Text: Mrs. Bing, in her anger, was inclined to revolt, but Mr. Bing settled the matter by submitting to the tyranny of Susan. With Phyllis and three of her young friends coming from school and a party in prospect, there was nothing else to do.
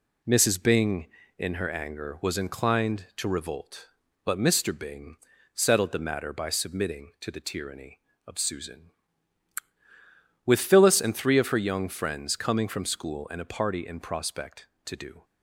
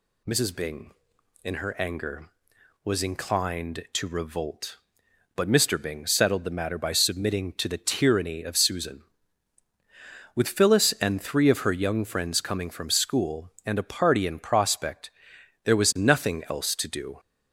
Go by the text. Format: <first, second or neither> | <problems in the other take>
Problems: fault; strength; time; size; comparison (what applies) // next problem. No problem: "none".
second | pauses between "Bing" and "settled"; slight; at 5.1 s; 0.36 s long // skips "there was nothing else"; at 14.7 s